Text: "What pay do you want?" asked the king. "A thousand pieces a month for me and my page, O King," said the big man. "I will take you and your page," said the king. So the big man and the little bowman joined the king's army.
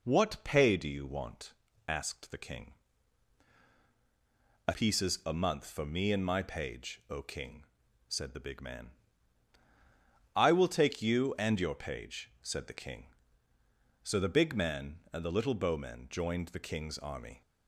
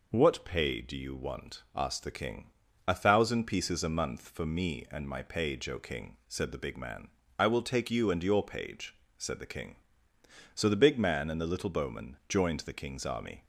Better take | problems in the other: second | skips "thousand"; at 4.7 s

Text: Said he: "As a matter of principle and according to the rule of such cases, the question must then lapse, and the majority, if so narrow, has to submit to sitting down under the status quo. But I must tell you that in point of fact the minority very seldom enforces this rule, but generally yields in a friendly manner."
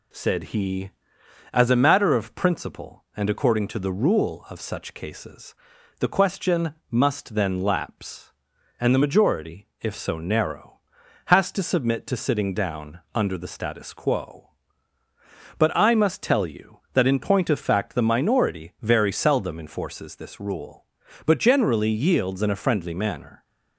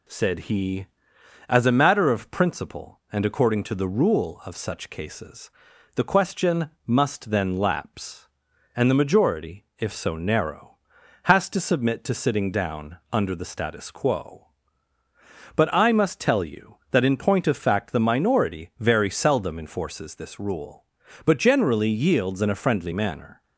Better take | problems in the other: neither | pauses between "question" and "must"; slight; the same in both

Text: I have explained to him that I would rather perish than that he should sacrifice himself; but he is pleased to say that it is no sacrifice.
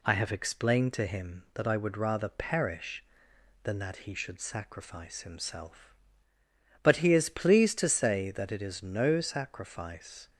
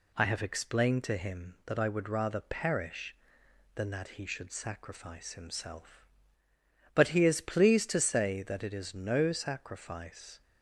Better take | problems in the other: neither | none

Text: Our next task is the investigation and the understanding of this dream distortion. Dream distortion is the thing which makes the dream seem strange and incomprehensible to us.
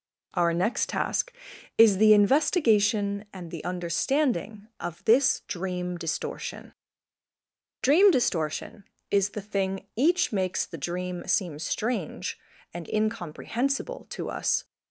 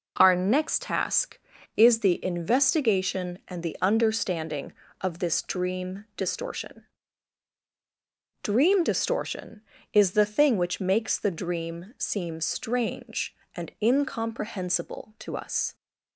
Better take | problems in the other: second | says "each" for "which"; at 9.9 s

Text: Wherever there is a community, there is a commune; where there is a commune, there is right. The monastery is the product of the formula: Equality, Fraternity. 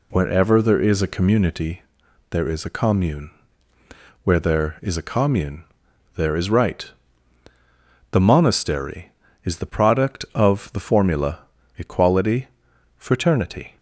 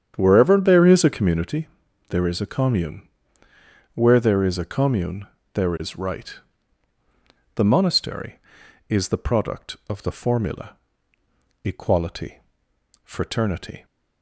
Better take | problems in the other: first | starts louder than the rest; strong; until 1.7 s; 8.5 dB

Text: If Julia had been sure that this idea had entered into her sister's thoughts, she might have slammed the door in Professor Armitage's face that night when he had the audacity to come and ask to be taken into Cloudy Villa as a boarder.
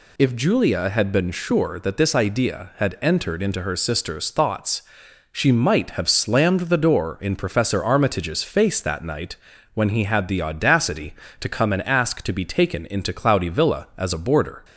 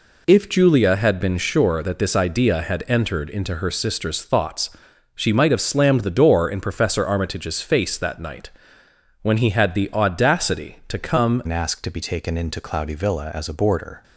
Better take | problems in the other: first | pauses between "night" and "when"; noticeable; at 8.4 s; 0.72 s long; also in the first // changes voice at "and"; from 11.4 s on; 2.6 s long

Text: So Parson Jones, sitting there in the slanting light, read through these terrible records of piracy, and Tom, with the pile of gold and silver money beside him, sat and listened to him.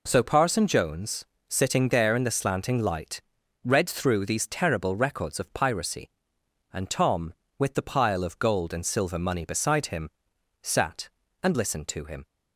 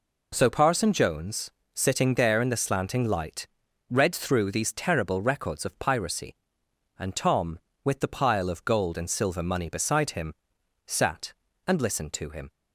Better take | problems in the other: neither | none

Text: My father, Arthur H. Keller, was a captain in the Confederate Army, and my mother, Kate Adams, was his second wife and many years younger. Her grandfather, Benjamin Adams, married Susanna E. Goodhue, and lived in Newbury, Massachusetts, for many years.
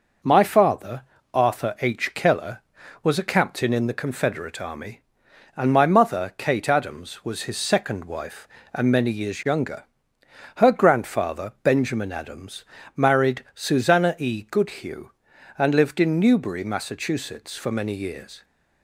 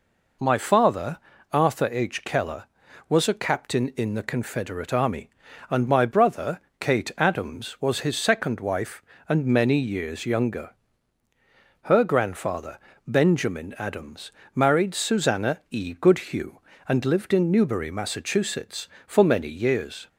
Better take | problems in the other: first | says "brother" for "mother"; at 6.0 s

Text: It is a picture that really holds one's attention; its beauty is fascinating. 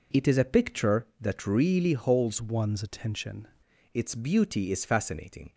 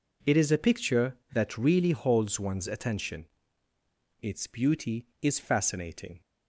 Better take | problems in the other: second | changes voice from "one's" to "attention"; from 2.4 to 3.4 s; 1.0 s long

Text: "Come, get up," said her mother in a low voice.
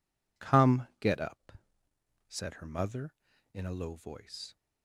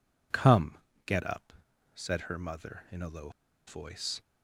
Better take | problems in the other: first | pauses between "low" and "voice"; at 3.2 s; 0.37 s long

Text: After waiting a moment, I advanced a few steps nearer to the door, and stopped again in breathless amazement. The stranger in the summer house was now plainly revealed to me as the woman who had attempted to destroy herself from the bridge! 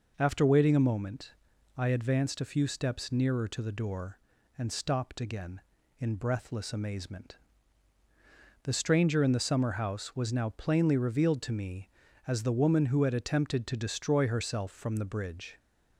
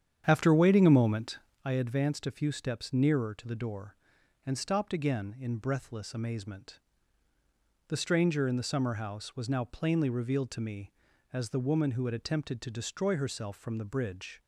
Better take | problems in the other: first | starts louder than the rest; strong; until 1.7 s; 9 dB

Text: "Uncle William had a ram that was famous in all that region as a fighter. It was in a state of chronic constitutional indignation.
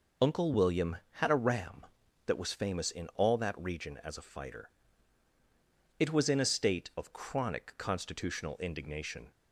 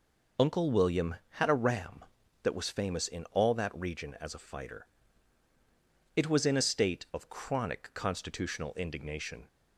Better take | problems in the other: neither | none

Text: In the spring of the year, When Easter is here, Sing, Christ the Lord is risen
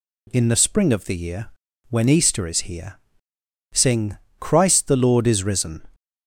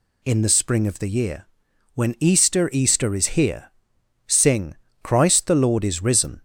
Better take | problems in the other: first | says "Easter" twice; at 2.7 s

